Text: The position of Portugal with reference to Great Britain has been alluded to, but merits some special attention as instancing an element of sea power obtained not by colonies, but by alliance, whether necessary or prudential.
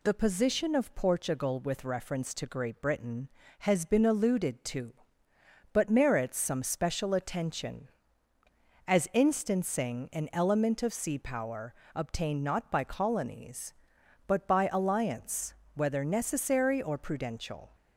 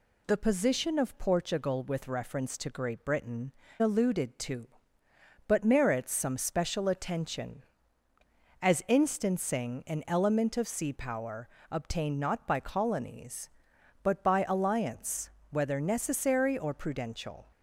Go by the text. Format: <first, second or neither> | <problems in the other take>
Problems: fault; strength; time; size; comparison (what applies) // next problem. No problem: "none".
first | skips "has been"; at 3.6 s // pauses between "power" and "obtained"; slight; at 11.4 s; 0.20 s long; slight in the first